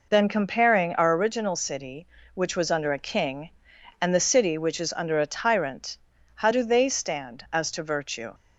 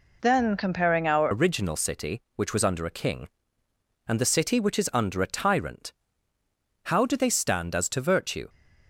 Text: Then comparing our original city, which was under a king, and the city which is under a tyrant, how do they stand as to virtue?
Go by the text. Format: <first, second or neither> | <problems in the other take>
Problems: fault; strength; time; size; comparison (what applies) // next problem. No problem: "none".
first | changes voice at "original"; from 1.3 s on; 7.1 s long